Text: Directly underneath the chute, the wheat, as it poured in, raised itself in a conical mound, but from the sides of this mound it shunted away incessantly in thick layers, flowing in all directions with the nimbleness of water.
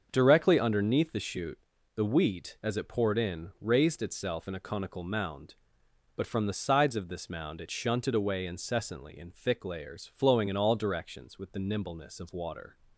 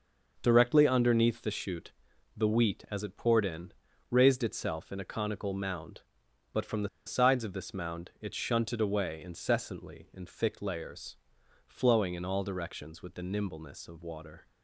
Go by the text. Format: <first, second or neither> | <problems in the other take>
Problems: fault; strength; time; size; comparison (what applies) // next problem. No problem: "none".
first | starts louder than the rest; until 1.4 s; 6 dB; also in the first // pauses between "the" and "sides"; slight; at 6.8 s; 0.17 s long